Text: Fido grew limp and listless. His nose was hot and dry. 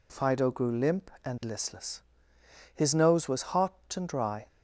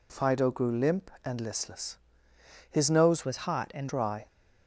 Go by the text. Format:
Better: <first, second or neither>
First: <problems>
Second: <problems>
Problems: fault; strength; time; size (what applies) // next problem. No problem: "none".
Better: first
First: none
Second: changes voice from "was" to "and"; from 3.2 to 3.8 s; 0.6 s long